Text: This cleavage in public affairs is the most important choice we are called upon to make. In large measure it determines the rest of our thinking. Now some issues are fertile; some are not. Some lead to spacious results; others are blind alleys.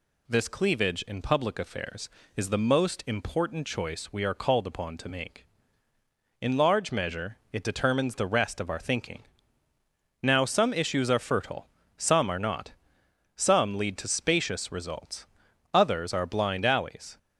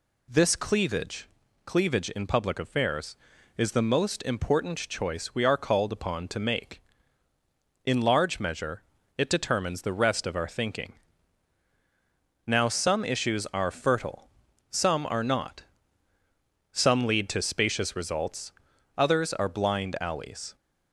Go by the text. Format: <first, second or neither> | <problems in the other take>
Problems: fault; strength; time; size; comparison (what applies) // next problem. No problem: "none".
first | says "cleavage" twice; at 1.6 s // pauses between "measure" and "it"; slight; at 8.8 s; 0.34 s long; slight in the first